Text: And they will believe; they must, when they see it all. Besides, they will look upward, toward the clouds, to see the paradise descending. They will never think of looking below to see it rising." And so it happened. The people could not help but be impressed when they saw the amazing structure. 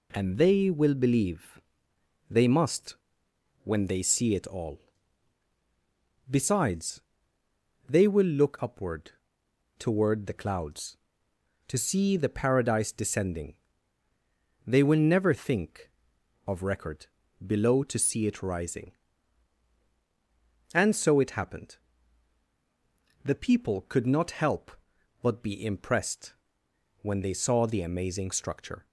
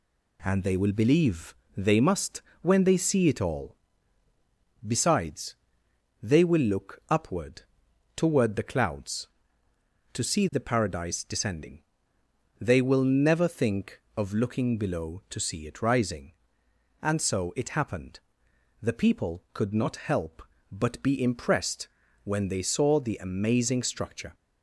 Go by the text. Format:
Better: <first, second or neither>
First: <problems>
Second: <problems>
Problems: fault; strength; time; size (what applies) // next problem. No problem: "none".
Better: second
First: says "record" for "looking"; at 16.6 s // pauses between "impressed" and "when"; noticeable; at 26.3 s; 0.68 s long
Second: pauses between "impressed" and "when"; slight; at 21.8 s; 0.36 s long